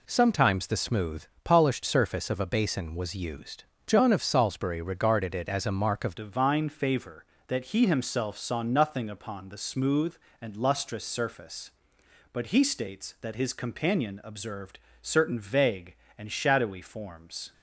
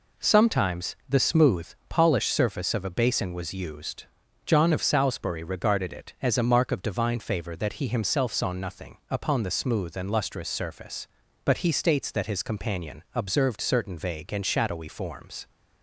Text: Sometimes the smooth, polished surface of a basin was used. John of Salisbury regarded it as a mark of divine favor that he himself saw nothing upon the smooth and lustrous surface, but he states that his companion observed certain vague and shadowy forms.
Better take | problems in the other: second | changes voice at "divine"; from 6.1 s on; 11.4 s long // pauses between "observed" and "certain"; slight; at 14.7 s; 0.22 s long

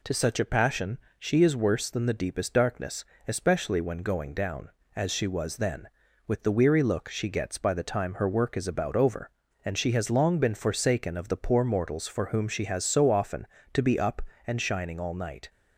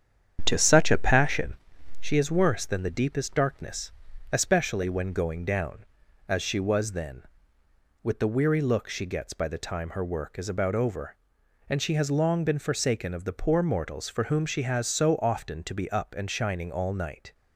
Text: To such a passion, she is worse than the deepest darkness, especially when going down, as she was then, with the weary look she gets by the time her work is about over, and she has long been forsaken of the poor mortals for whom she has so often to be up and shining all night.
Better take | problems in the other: first | starts louder than the rest; strong; until 1.6 s; 8.5 dB

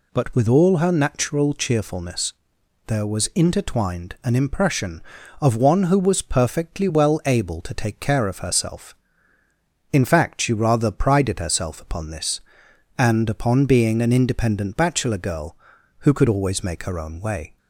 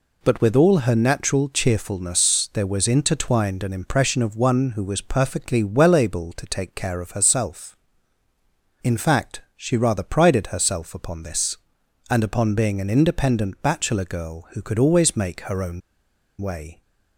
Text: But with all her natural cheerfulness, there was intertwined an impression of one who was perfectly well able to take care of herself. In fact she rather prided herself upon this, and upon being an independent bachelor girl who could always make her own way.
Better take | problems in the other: first | pauses between "fact" and "she"; slight; at 9.4 s; 0.16 s long // pauses between "own" and "way"; noticeable; at 15.8 s; 0.60 s long

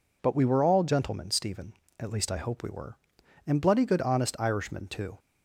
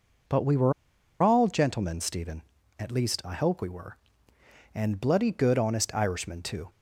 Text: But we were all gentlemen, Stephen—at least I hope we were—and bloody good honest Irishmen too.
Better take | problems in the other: first | pauses between "were" and "all"; noticeable; at 0.7 s; 0.49 s long

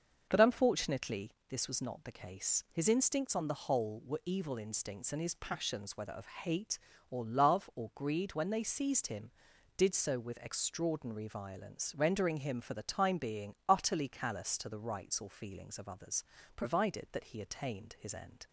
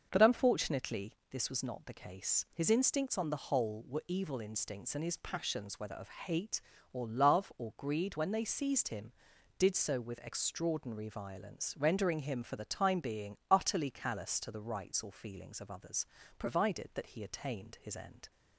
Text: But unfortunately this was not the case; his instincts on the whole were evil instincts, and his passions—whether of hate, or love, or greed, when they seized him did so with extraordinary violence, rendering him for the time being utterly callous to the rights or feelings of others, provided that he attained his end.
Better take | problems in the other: neither | starts louder than the rest; the same in both // pauses between "unfortunately" and "this"; slight; the same in both

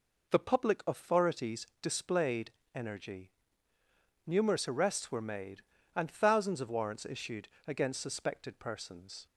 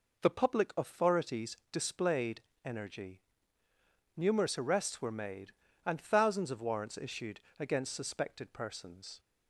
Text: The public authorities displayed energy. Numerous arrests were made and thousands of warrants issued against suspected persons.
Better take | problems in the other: neither | pauses between "authorities" and "displayed"; slight; the same in both // pauses between "displayed" and "energy"; slight; the same in both // pauses between "issued" and "against"; slight; the same in both

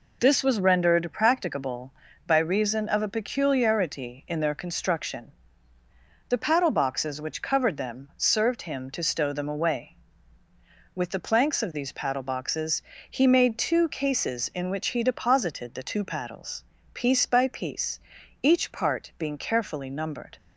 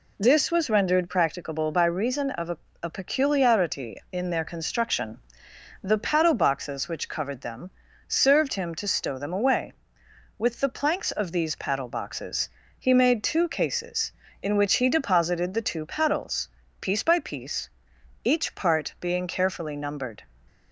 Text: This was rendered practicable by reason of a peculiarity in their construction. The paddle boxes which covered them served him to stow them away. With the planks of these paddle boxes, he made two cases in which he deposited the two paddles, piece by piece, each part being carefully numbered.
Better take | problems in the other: first | says "a" twice; at 2.8 s // pauses between "them" and "served"; at 7.6 s; 0.38 s long

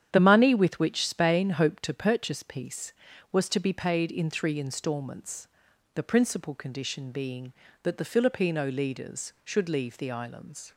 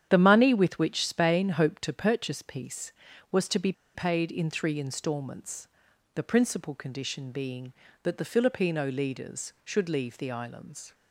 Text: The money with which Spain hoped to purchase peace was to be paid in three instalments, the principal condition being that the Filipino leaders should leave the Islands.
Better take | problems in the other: first | starts louder than the rest; strong; until 1.1 s; 9.5 dB; strong in the first // pauses between "be" and "paid"; slight; at 3.7 s; 0.22 s long

